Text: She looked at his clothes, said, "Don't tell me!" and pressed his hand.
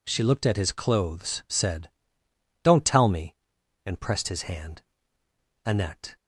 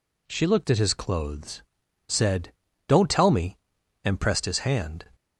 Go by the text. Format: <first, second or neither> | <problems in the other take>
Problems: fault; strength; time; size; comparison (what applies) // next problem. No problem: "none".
second | goes on to say "Annette"; from 5.6 s on; 0.50 s long